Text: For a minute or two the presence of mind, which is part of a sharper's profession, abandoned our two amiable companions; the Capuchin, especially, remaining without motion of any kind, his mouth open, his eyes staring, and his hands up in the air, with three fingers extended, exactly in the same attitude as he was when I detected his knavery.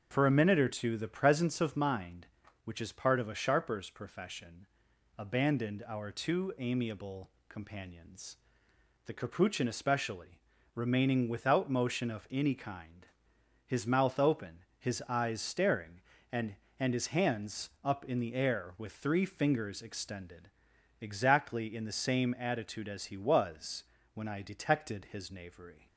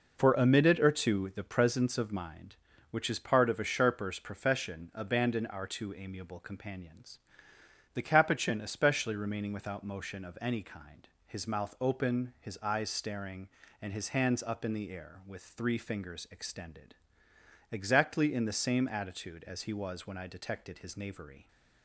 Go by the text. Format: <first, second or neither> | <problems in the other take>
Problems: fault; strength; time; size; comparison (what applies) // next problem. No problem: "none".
second | starts louder than the rest; until 1.1 s; 6.5 dB // pauses between "amiable" and "companions"; slight; at 7.2 s; 0.18 s long // says "and" twice; at 16.7 s // pauses between "was" and "when"; slight; at 23.8 s; 0.28 s long